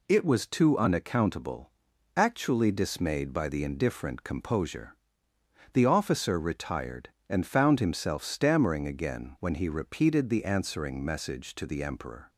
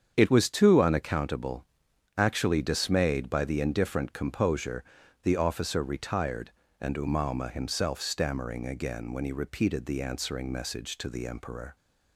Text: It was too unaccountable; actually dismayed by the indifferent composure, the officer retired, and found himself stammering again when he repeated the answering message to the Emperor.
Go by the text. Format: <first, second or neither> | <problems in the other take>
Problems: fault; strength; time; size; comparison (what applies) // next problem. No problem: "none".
first | starts louder than the rest; strong; until 1.1 s; 7.5 dB // says "umauma" for "found"; at 6.9 s